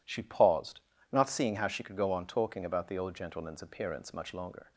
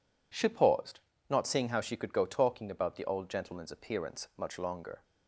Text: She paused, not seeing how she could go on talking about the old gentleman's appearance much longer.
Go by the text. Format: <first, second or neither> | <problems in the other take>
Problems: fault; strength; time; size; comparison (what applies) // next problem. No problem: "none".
first | skips "on"; at 2.2 s